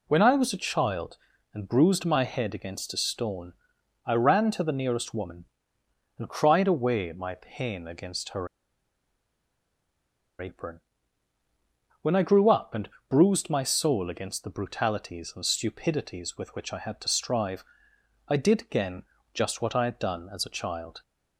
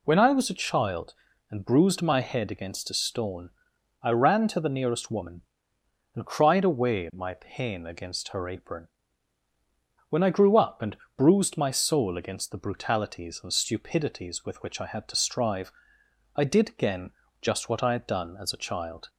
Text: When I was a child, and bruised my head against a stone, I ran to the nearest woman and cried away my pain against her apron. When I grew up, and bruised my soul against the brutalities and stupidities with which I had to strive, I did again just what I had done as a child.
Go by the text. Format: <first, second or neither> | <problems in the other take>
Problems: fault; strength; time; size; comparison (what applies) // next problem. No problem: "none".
second | pauses between "her" and "apron"; strong; at 8.4 s; 1.9 s long // pauses between "and" and "bruised"; slight; at 12.8 s; 0.22 s long; slight in the second // pauses between "again" and "just"; slight; at 19.0 s; 0.30 s long; slight in the second